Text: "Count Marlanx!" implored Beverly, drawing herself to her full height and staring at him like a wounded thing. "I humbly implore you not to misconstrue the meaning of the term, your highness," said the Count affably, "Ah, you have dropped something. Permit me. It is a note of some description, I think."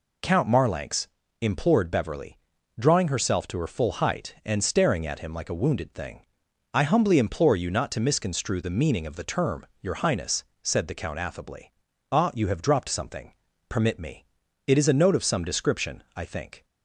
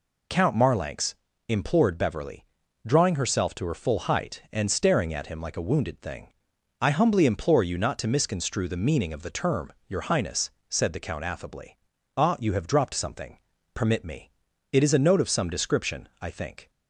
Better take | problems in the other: neither | none

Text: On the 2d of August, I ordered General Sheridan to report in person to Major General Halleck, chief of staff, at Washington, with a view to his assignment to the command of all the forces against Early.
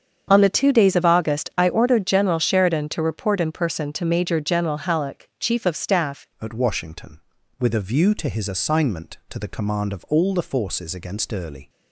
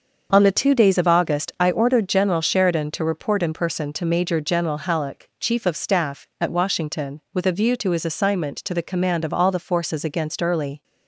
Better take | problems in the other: second | starts louder than the rest; strong; until 1.3 s; 7.5 dB; also in the second // changes voice at "at"; from 6.4 s on; 5.2 s long

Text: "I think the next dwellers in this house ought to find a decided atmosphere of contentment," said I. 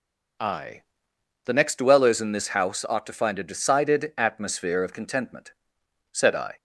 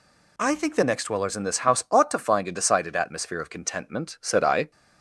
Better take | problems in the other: second | skips "think"; at 1.1 s

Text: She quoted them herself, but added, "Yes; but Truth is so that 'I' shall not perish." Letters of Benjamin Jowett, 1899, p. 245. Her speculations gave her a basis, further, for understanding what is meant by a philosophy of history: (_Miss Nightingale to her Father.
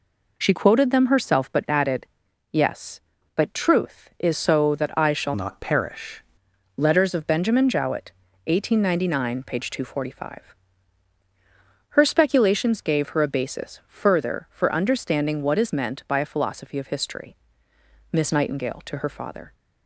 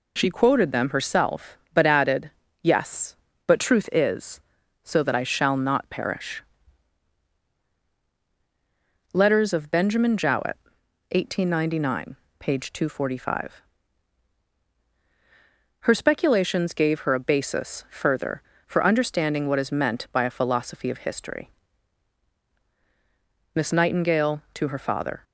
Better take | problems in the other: second | changes voice from "not" to "perish"; from 5.3 to 6.2 s; 0.9 s long

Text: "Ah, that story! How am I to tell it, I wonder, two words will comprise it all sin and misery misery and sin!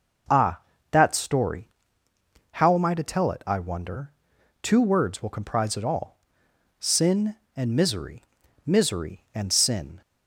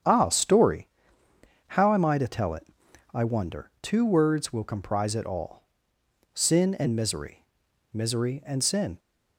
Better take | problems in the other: first | starts louder than the rest; strong; until 1.8 s; 8 dB // skips "that"; at 0.2 s // pauses between "all" and "sin"; noticeable; at 5.6 s; 0.72 s long; noticeable in the first // pauses between "misery" and "misery"; noticeable; at 7.4 s; 0.48 s long; also in the first

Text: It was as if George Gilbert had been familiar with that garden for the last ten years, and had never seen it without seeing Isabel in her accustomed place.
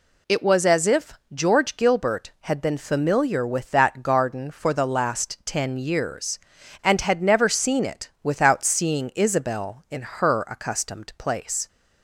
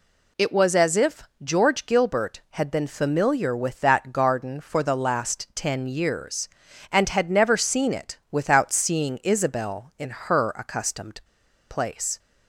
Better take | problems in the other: first | pauses between "if" and "George"; slight; at 1.2 s; 0.20 s long; slight in the first // pauses between "accustomed" and "place"; noticeable; at 11.1 s; 0.50 s long

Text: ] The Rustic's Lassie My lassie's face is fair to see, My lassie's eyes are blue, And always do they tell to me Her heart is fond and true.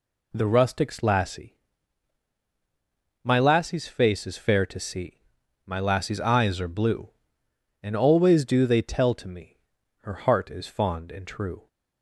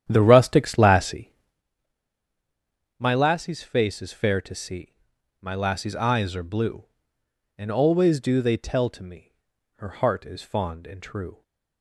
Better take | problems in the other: first | starts louder than the rest; strong; until 1.6 s; 10 dB // pauses between "Lassie" and "My"; strong; at 1.3 s; 1.6 s long; strong in the first // pauses between "me" and "Her"; noticeable; at 9.3 s; 0.46 s long; noticeable in the first

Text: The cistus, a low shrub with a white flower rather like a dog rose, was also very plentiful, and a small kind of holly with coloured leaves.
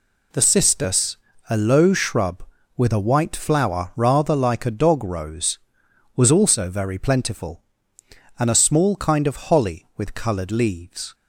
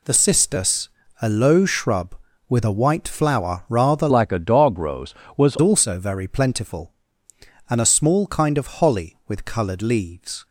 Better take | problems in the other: first | changes voice from "like" to "was"; from 4.1 to 5.5 s; 1.4 s long

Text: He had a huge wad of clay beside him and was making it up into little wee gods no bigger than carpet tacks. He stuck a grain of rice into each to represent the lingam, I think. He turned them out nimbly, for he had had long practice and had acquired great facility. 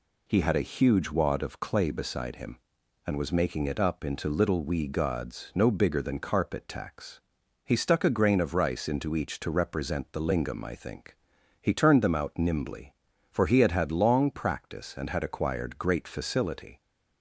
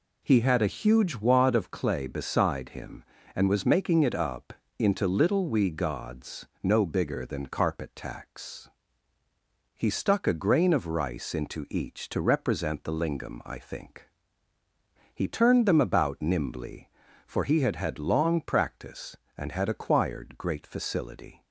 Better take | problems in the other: first | pauses between "up" and "into"; slight; at 4.5 s; 0.24 s long // pauses between "gods" and "no"; slight; at 6.4 s; 0.18 s long // says "about" for "out"; at 15.8 s

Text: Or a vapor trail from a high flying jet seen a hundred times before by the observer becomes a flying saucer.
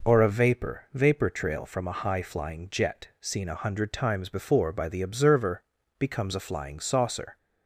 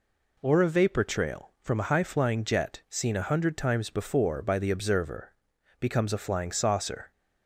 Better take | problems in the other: second | says "vapor" twice; at 0.9 s // pauses between "observer" and "becomes"; at 5.6 s; 0.38 s long; noticeable in the second

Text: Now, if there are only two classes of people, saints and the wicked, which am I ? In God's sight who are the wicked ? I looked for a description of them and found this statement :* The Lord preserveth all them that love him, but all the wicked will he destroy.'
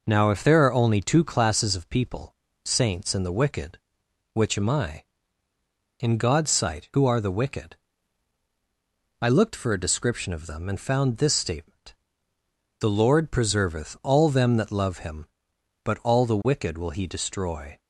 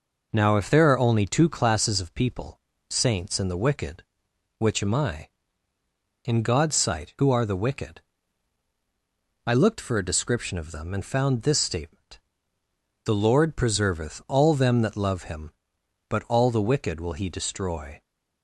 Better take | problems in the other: neither | none

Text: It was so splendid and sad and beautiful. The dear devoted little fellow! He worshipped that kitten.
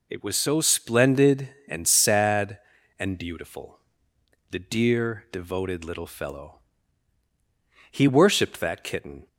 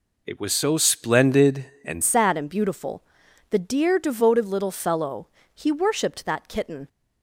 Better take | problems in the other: first | changes voice at "sad"; from 2.0 s on; 4.8 s long

